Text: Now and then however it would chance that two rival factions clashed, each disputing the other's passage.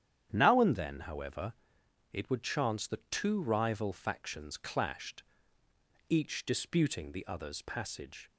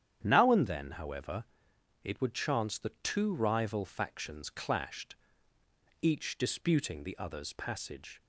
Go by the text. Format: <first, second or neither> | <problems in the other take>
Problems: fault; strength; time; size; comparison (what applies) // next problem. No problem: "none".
neither | starts louder than the rest; strong; the same in both // pauses between "however" and "it"; noticeable; the same in both